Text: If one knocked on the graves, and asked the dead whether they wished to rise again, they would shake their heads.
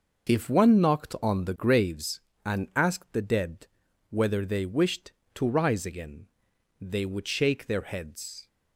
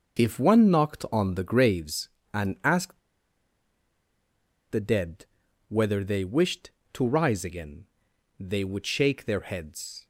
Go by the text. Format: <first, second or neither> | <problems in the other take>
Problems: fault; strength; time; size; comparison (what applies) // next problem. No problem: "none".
first | pauses between "asked" and "the"; strong; at 2.9 s; 1.7 s long // pauses between "dead" and "whether"; noticeable; at 5.2 s; 0.46 s long; noticeable in the first